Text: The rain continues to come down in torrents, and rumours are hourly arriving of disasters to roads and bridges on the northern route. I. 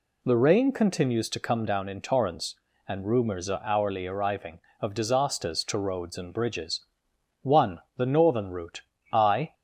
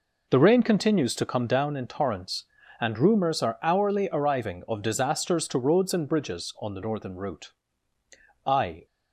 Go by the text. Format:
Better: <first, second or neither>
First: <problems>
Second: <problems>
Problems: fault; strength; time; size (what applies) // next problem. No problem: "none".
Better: second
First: says "one" for "on"; at 7.4 s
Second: none